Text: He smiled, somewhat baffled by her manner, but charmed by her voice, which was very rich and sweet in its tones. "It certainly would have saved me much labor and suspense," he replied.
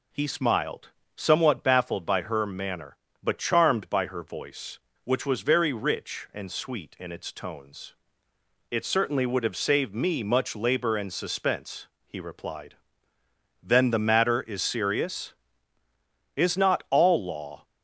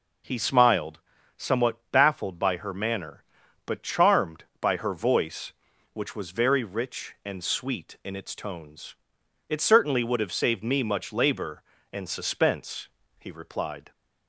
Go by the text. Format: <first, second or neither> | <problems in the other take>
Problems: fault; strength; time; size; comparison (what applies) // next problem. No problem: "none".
second | goes on to say "Then the matter is serious Is not all law"; strong; from 13.6 s on; 4.0 s long